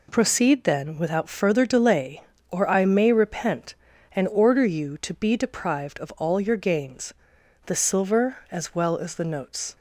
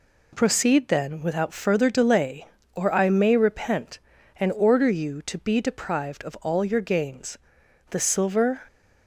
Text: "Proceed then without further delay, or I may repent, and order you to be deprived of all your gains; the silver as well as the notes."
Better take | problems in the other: first | stops before "as well as the notes"; at 8.6 s

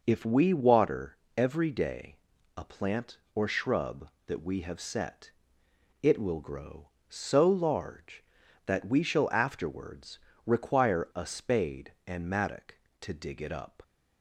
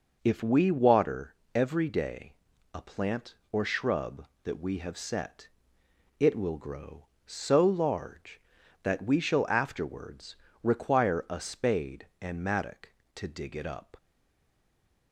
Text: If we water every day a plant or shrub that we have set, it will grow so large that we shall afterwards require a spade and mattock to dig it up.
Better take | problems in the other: first | pauses between "water" and "every"; slight; at 1.3 s; 0.22 s long; slight in the first // pauses between "day" and "a"; at 2.3 s; 0.42 s long; also in the first // pauses between "afterwards" and "require"; slight; at 10.3 s; 0.26 s long; slight in the first // stays silent after the last word; from 13.9 s on; 1.2 s long

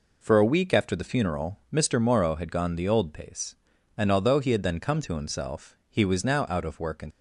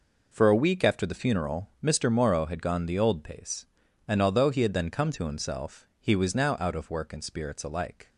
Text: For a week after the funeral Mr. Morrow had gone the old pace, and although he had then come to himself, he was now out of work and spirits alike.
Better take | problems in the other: second | stops before "spirits alike"; at 7.1 s

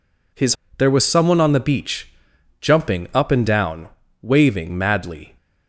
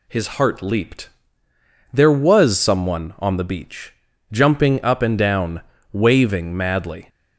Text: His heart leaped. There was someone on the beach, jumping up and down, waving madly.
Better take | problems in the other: second | skips "heart leaped"; at 0.6 s

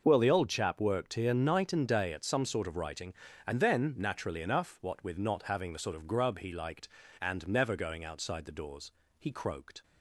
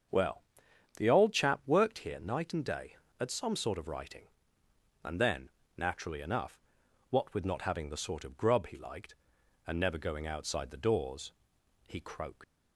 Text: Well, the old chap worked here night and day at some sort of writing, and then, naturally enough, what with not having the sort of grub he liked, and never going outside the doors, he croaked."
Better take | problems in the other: first | starts louder than the rest; until 1.6 s; 6.5 dB // leaves "croaked" unfinished; at 12.4 s; 110 ms

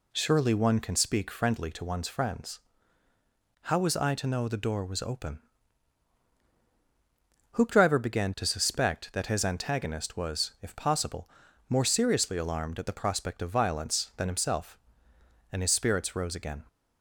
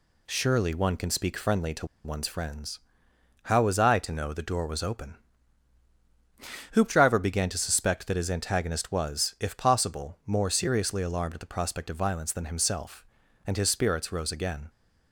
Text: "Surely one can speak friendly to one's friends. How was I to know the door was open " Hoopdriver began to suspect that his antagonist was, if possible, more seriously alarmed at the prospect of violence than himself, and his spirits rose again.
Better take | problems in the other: first | pauses between "to" and "one's"; slight; at 1.8 s; 0.17 s long

